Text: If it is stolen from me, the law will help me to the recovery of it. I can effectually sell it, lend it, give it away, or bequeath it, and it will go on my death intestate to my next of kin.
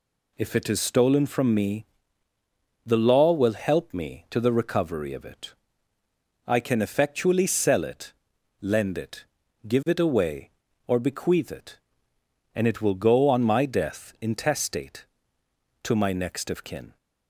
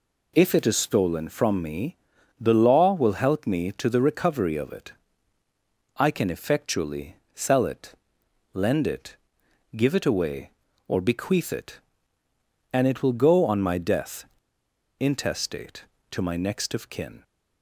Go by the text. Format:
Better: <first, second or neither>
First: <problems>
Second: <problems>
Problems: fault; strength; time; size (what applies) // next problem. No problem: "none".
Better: first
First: none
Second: pauses between "effectually" and "sell"; slight; at 7.1 s; 0.20 s long // pauses between "death" and "intestate"; noticeable; at 14.2 s; 0.74 s long